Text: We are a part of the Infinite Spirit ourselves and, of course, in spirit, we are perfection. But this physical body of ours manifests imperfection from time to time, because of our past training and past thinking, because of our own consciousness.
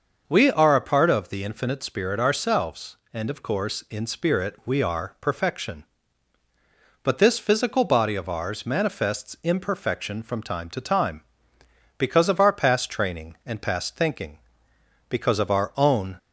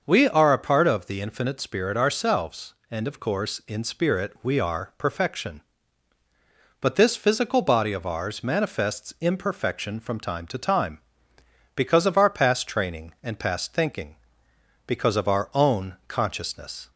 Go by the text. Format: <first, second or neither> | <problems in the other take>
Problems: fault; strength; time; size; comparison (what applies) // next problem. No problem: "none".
second | starts louder than the rest; noticeable; until 1.2 s; 6 dB; noticeable in the second // stops before "consciousness"; at 16.1 s